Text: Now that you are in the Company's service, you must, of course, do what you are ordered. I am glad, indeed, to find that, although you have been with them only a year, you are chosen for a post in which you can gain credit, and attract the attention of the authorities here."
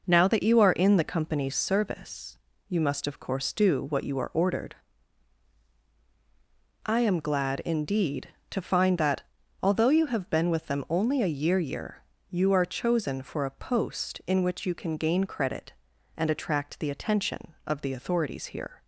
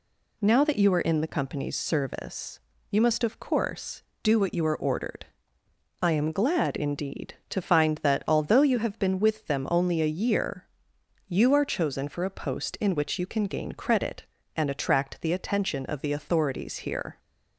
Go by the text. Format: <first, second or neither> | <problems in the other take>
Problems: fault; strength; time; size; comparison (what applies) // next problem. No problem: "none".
second | says "year" twice; at 11.5 s